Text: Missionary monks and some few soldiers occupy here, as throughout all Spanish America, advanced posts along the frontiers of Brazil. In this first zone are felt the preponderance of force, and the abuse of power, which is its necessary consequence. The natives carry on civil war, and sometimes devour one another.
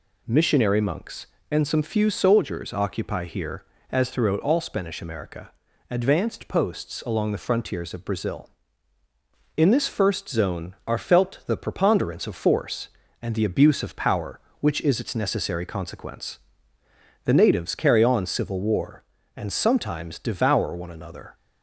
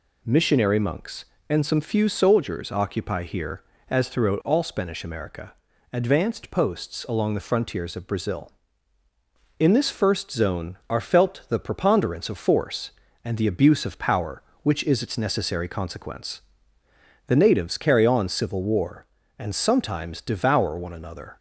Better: neither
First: none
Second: none

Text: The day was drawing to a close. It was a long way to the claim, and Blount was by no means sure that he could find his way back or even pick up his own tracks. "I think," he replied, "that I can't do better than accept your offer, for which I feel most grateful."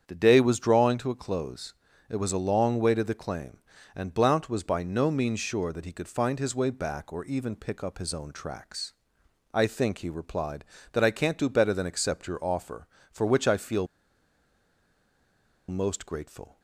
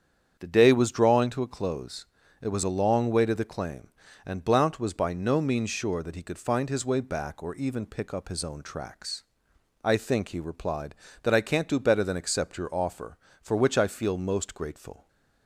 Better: second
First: starts louder than the rest; strong; until 1.0 s; 8 dB // pauses between "feel" and "most"; strong; at 13.8 s; 1.8 s long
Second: starts louder than the rest; strong; until 1.4 s; 8 dB

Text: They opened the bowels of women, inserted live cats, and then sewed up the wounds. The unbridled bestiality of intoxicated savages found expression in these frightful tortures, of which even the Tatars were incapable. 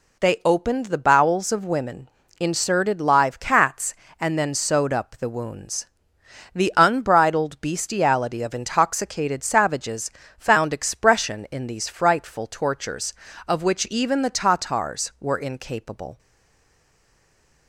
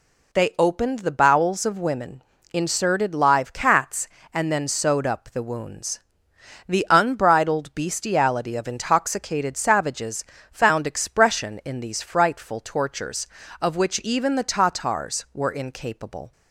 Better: second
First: pauses between "savages" and "found"; slight; at 10.0 s; 0.28 s long // stays silent after the last word; noticeable; from 16.1 s on; 1.5 s long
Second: pauses between "savages" and "found"; slight; at 10.2 s; 0.28 s long

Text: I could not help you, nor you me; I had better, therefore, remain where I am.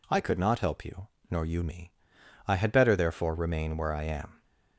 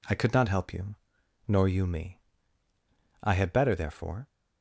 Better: first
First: none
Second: stops before "remain where I am"; at 4.2 s

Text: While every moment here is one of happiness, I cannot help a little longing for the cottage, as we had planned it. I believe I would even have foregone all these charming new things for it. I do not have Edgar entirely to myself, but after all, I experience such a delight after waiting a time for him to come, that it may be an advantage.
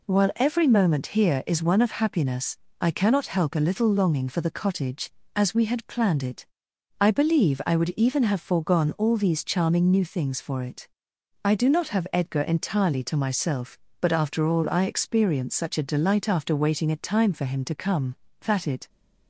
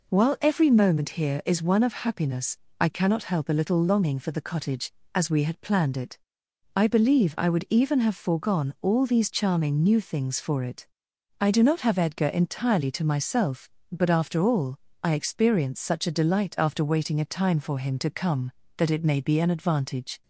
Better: second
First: stops before "may be an advantage"; at 18.8 s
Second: none

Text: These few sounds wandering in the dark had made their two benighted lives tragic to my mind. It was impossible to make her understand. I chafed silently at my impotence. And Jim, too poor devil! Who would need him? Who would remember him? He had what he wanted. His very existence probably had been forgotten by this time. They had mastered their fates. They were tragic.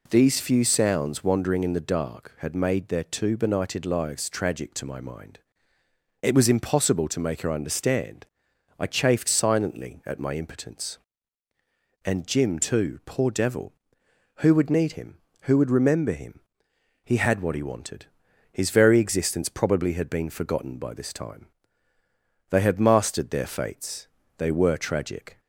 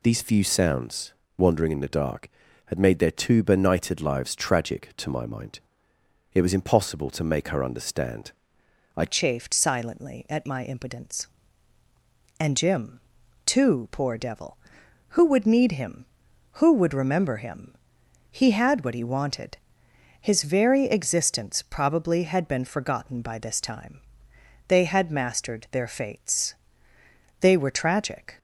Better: first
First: none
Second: pauses between "sounds" and "wandering"; slight; at 1.1 s; 0.24 s long // changes voice at "chafed"; from 9.0 s on; 19.3 s long

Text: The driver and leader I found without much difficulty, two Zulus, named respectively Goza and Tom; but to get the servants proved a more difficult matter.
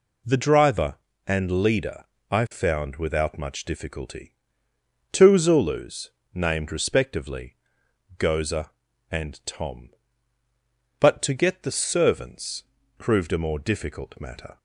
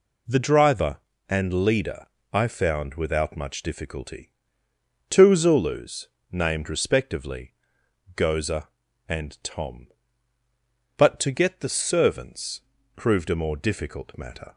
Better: neither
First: pauses between "leader" and "I"; slight; at 2.0 s; 0.26 s long // pauses between "respectively" and "Goza"; noticeable; at 7.5 s; 0.62 s long // pauses between "servants" and "proved"; slight; at 12.6 s; 0.34 s long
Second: pauses between "leader" and "I"; slight; at 2.0 s; 0.26 s long // pauses between "respectively" and "Goza"; noticeable; at 7.5 s; 0.62 s long // pauses between "servants" and "proved"; slight; at 12.6 s; 0.34 s long

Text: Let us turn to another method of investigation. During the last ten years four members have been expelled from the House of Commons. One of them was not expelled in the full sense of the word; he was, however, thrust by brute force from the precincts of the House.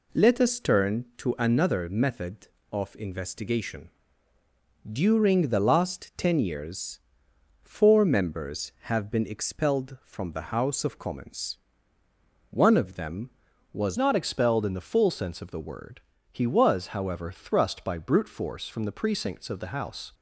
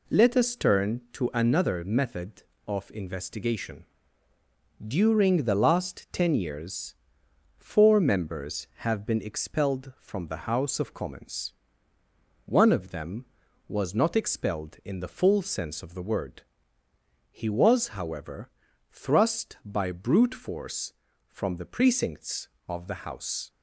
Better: second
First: pauses between "years" and "four"; noticeable; at 6.9 s; 0.64 s long // changes voice at "not"; from 13.9 s on; 6.2 s long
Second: pauses between "years" and "four"; noticeable; at 6.9 s; 0.64 s long

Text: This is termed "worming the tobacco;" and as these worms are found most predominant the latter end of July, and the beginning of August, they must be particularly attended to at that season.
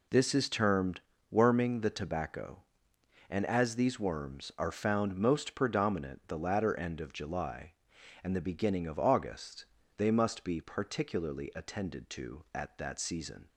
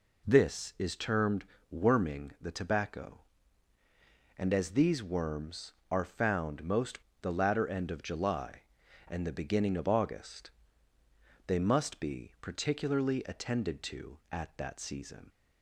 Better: first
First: pauses between "termed" and "worming"; slight; at 1.0 s; 0.28 s long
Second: pauses between "termed" and "worming"; slight; at 1.4 s; 0.26 s long // skips "predominant"; at 7.1 s

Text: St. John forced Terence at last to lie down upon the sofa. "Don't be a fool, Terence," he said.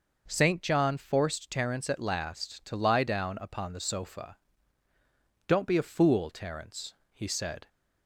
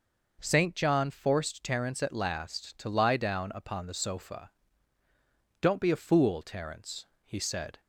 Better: neither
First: none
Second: none

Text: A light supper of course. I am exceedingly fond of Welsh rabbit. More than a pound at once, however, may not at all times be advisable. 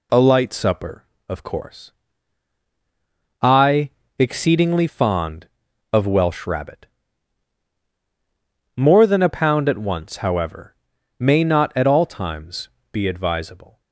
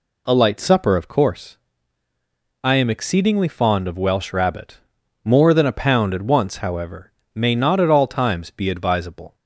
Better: second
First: skips "am"; at 4.0 s // pauses between "times" and "be"; slight; at 12.6 s; 0.24 s long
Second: none

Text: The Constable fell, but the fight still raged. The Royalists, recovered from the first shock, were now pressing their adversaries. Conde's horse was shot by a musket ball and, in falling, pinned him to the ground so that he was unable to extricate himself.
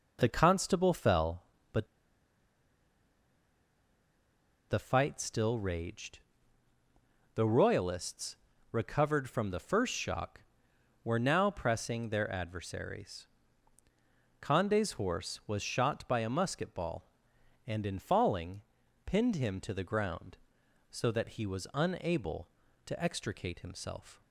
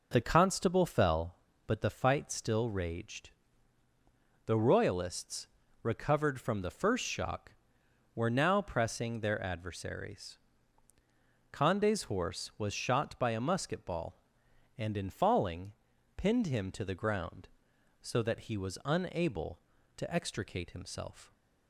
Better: second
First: pauses between "but" and "the"; strong; at 1.8 s; 2.8 s long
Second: none

